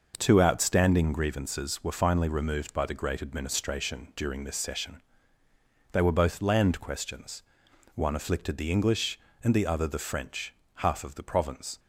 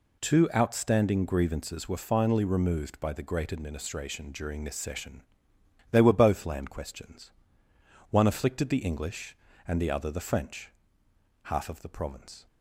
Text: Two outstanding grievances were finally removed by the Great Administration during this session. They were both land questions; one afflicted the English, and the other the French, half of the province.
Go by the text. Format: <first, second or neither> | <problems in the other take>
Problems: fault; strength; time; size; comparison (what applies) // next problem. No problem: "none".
neither | none